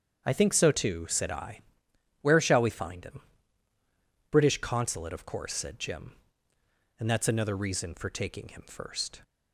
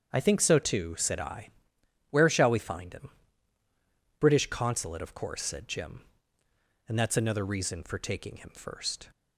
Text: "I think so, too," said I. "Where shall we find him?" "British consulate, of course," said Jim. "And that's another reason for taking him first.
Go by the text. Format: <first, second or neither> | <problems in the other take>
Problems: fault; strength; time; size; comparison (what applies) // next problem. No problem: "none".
neither | starts louder than the rest; strong; the same in both